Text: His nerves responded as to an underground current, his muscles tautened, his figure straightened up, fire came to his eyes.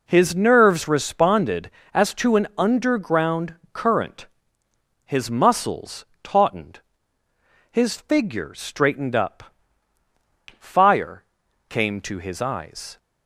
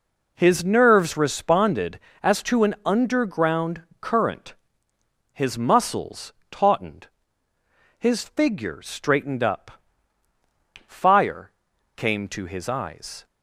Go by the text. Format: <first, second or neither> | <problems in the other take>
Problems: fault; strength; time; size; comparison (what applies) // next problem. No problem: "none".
neither | pauses between "underground" and "current"; slight; the same in both // pauses between "muscles" and "tautened"; slight; the same in both // pauses between "fire" and "came"; noticeable; the same in both